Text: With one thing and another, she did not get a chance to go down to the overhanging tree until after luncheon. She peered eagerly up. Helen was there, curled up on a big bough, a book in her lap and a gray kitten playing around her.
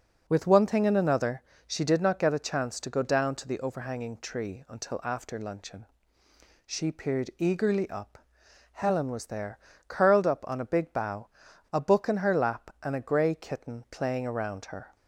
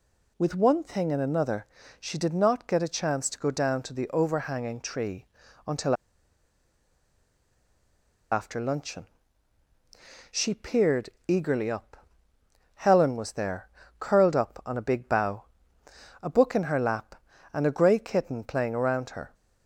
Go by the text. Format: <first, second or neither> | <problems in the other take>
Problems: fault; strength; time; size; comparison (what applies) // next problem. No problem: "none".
first | pauses between "tree" and "until"; at 5.2 s; 0.42 s long // pauses between "until" and "after"; strong; at 5.9 s; 2.3 s long // pauses between "peered" and "eagerly"; slight; at 11.0 s; 0.18 s long